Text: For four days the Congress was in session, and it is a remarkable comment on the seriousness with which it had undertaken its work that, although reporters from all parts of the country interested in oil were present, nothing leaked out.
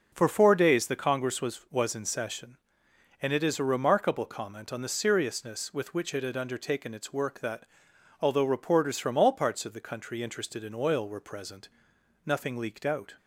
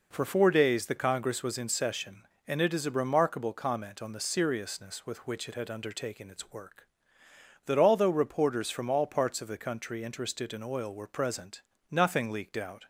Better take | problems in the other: second | says "was" twice; at 1.7 s

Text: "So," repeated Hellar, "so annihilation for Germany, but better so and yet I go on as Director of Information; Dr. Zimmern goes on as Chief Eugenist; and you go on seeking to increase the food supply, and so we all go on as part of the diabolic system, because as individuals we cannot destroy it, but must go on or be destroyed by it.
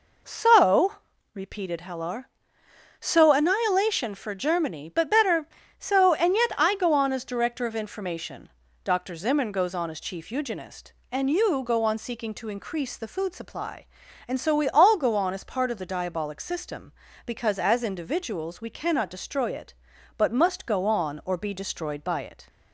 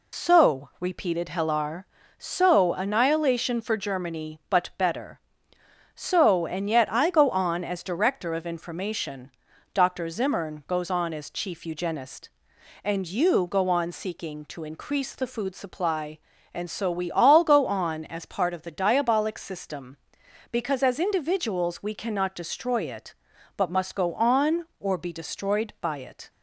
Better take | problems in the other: first | loses the start of "So"; at 0.1 s; 85 ms

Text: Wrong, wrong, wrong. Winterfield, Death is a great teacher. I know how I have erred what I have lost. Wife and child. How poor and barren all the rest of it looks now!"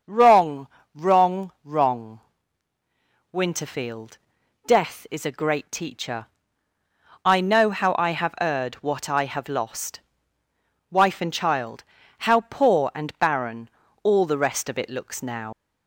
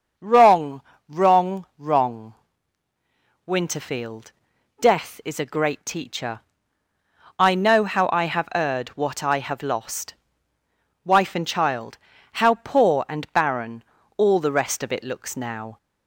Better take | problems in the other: second | starts louder than the rest; until 1.3 s; 6.5 dB; also in the second // pauses between "barren" and "all"; slight; at 13.6 s; 0.34 s long; slight in the second // leaves "now" unfinished; at 15.5 s; 100 ms

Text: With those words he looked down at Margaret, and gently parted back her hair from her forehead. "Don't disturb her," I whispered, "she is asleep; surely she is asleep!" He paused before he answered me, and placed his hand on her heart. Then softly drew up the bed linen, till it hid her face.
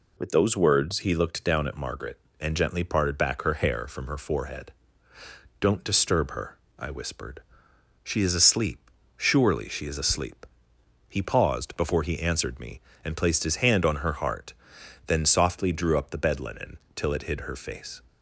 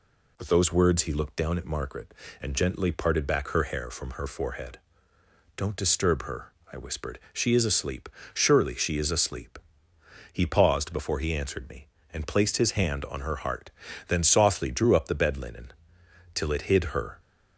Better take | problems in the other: first | stops before "face"; at 17.1 s

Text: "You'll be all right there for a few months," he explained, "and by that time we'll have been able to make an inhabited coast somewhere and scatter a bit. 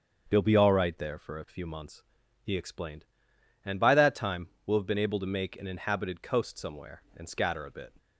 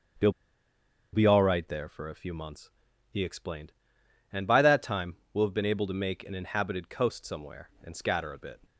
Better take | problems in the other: first | starts louder than the rest; until 2.0 s; 7 dB; also in the first // pauses between "You'll" and "be"; noticeable; at 0.3 s; 0.81 s long // pauses between "time" and "we'll"; slight; at 5.1 s; 0.16 s long; slight in the first

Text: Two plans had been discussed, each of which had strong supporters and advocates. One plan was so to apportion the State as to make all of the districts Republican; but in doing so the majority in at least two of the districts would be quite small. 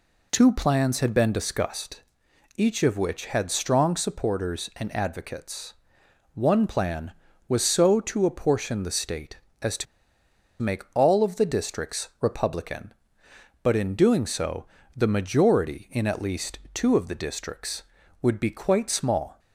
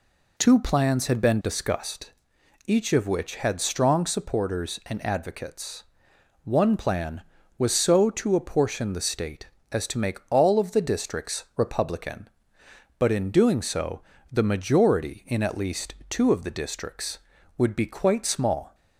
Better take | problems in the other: second | pauses between "to" and "make"; noticeable; at 9.8 s; 0.77 s long // pauses between "so" and "the"; slight; at 14.6 s; 0.32 s long; slight in the second // pauses between "least" and "two"; slight; at 16.5 s; 0.16 s long; slight in the second

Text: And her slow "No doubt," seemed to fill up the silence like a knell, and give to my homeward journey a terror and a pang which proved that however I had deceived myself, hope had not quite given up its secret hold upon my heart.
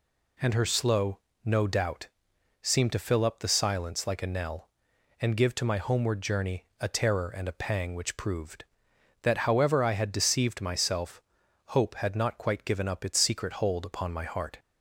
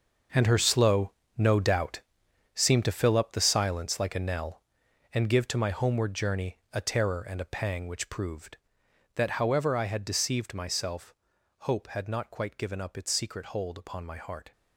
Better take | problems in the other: first | gets quieter; strong; throughout; 12.5 dB // pauses between "slow" and "No"; slight; at 1.1 s; 0.26 s long; slight in the first

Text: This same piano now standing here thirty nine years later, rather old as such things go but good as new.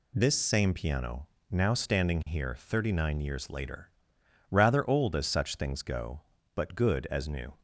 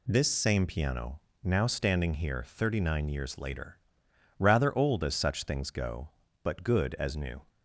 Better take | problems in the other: neither | pauses between "piano" and "now"; slight; the same in both

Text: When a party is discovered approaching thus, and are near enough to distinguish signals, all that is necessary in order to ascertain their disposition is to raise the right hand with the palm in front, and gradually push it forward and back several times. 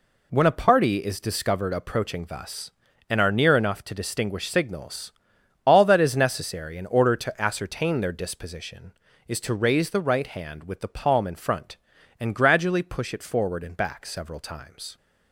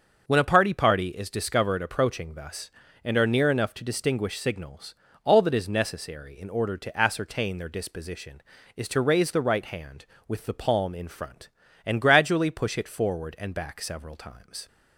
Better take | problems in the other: first | starts louder than the rest; until 1.2 s; 6.5 dB // says "party" twice; at 0.7 s

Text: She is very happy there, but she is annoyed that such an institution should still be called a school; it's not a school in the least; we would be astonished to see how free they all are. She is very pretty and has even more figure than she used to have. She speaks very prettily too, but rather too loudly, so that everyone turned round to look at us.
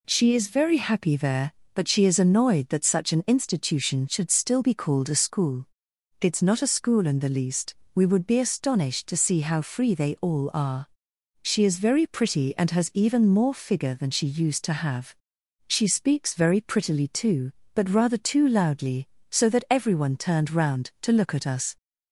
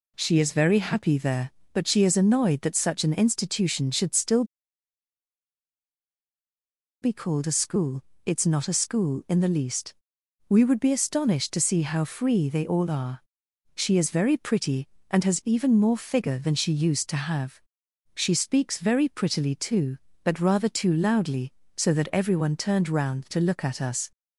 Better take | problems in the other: first | pauses between "still" and "be"; strong; at 4.4 s; 2.5 s long

